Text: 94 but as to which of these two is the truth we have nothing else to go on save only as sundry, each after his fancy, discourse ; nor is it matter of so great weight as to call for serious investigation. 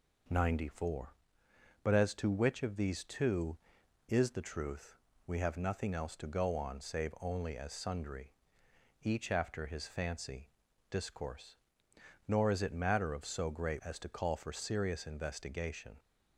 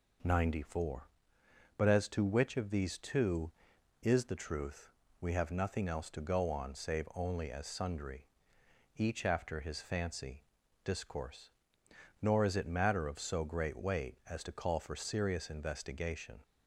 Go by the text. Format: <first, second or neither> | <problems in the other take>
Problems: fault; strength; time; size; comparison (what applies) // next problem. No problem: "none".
second | pauses between "truth" and "we"; slight; at 4.9 s; 0.28 s long; slight in the second // skips "weight"; at 13.8 s